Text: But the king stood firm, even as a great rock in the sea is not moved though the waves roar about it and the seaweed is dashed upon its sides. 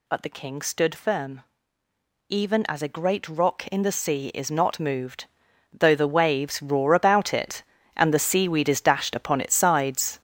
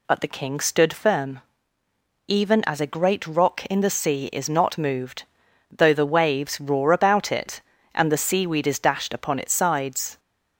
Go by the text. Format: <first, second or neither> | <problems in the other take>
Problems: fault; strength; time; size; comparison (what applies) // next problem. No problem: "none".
second | gets louder; strong; throughout; 8.5 dB // pauses between "moved" and "though"; noticeable; at 5.2 s; 0.48 s long; noticeable in the second